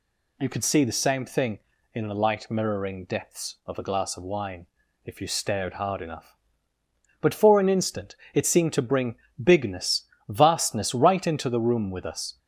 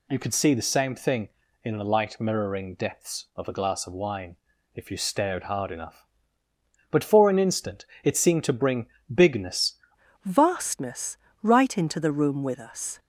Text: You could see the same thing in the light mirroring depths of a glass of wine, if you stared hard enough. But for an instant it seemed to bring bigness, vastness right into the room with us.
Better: first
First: pauses between "instant" and "it"; slight; at 8.1 s; 0.18 s long // pauses between "bring" and "bigness"; slight; at 9.1 s; 0.26 s long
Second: pauses between "instant" and "it"; slight; at 7.8 s; 0.18 s long // pauses between "bring" and "bigness"; slight; at 8.8 s; 0.26 s long // changes voice at "vastness"; from 10.2 s on; 2.7 s long // pauses between "vastness" and "right"; slight; at 11.1 s; 0.26 s long

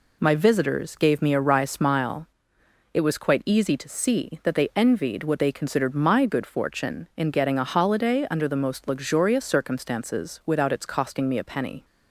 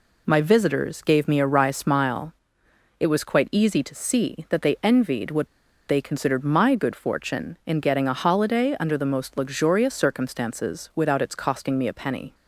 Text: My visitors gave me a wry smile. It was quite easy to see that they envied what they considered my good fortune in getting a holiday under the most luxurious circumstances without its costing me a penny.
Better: first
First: none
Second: pauses between "what" and "they"; at 5.4 s; 0.42 s long

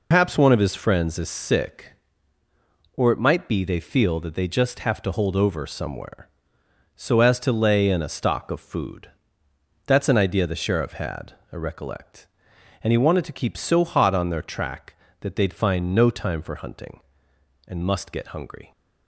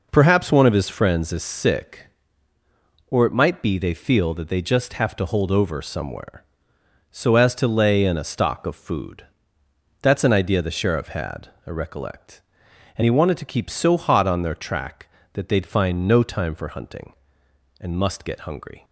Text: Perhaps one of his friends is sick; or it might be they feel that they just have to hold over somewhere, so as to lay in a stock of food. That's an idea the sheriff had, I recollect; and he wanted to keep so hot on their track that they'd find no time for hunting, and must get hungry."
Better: second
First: loses the start of "Perhaps"; at 0.1 s; 140 ms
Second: none

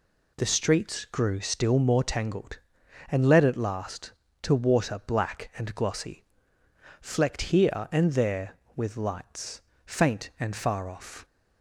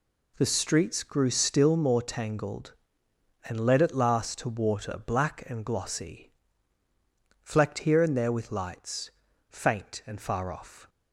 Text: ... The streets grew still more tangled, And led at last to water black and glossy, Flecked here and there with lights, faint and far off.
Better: neither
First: none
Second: none

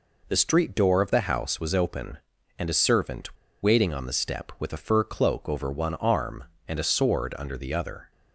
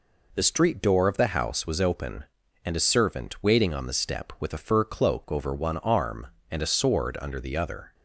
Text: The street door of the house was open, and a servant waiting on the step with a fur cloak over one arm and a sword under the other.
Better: second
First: pauses between "servant" and "waiting"; slight; at 3.3 s; 0.26 s long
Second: none

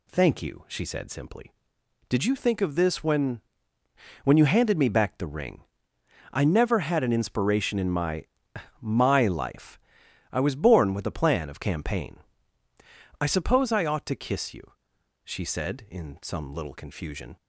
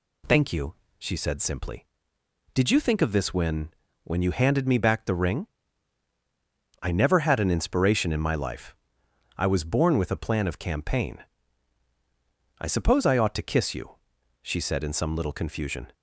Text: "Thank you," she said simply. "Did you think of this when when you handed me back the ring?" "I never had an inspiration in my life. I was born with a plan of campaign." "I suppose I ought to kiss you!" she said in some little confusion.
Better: second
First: pauses between "when" and "when"; noticeable; at 3.4 s; 0.82 s long // says "my" twice; at 8.7 s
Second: pauses between "when" and "when"; slight; at 3.7 s; 0.34 s long

